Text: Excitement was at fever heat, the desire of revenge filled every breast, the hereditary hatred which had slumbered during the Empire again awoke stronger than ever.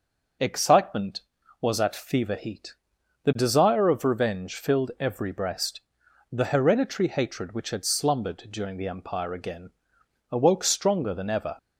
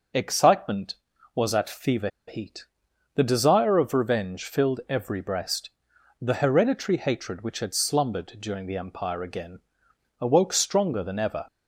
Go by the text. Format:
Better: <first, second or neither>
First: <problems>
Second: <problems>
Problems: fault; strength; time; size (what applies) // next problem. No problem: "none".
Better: first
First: pauses between "again" and "awoke"; noticeable; at 9.7 s; 0.60 s long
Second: pauses between "fever" and "heat"; slight; at 2.0 s; 0.19 s long // pauses between "again" and "awoke"; noticeable; at 9.5 s; 0.60 s long